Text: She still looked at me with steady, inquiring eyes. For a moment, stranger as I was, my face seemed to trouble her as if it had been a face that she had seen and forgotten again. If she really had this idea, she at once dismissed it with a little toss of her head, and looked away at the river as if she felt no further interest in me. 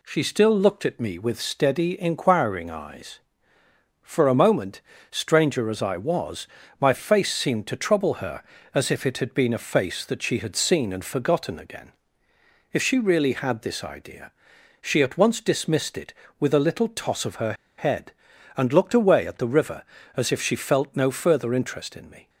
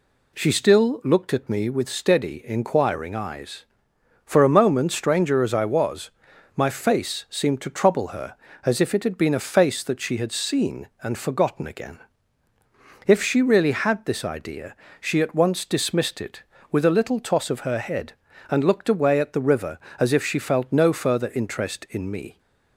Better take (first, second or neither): second